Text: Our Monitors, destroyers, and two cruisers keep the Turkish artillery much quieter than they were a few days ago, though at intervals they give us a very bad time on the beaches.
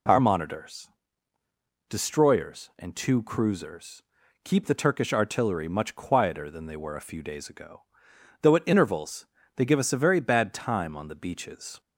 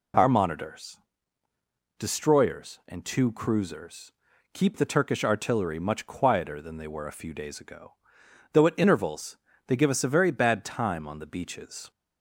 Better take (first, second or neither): neither